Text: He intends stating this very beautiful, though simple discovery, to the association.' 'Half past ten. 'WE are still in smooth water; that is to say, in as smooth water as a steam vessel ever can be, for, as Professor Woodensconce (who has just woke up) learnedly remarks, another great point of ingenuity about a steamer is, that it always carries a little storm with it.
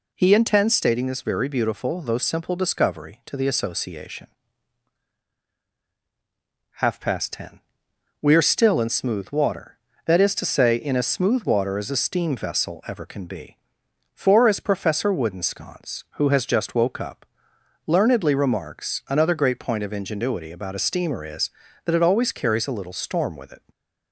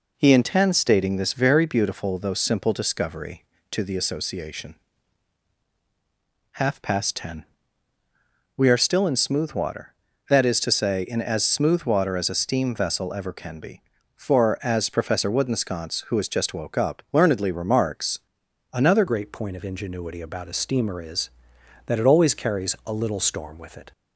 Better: first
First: none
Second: changes voice at "great"; from 19.0 s on; 4.9 s long

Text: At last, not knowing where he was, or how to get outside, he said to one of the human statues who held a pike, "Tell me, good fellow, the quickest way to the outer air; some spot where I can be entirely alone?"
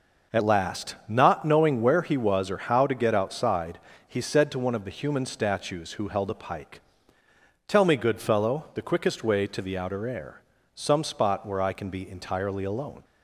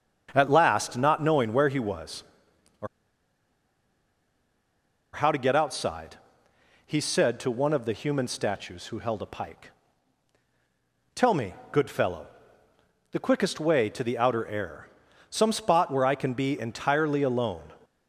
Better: first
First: none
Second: starts louder than the rest; until 1.3 s; 6.5 dB // pauses between "or" and "how"; strong; at 2.8 s; 2.2 s long

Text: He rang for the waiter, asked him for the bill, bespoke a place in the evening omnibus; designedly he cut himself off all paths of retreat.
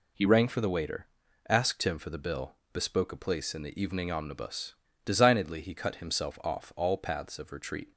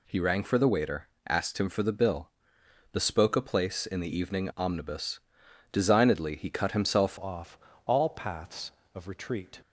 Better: first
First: none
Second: changes voice at "off"; from 7.1 s on; 2.5 s long // pauses between "off" and "all"; slight; at 7.5 s; 0.26 s long

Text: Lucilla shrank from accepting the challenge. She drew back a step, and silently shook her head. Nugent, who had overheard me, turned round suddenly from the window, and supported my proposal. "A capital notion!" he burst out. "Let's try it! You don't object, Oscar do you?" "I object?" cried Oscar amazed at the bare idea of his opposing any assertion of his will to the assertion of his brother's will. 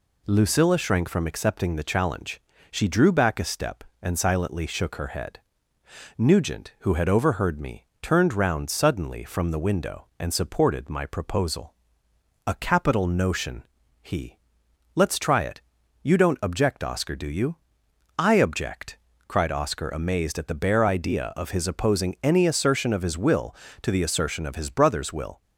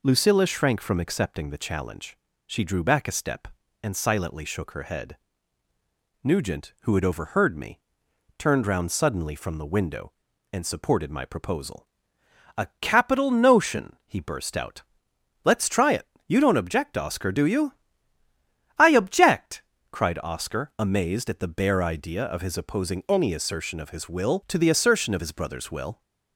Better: second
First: skips "burst out"; at 14.6 s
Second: none

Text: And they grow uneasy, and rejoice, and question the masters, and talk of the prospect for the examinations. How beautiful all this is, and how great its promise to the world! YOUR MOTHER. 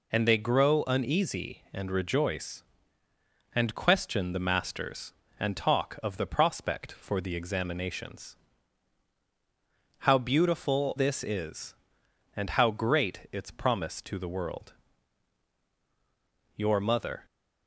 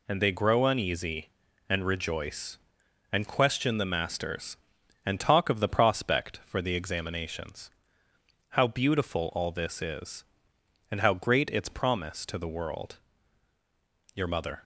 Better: second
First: skips "all"; at 10.9 s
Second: none

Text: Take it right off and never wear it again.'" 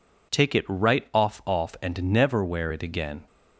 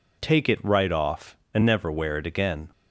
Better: second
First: says "off" twice; at 1.4 s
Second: none

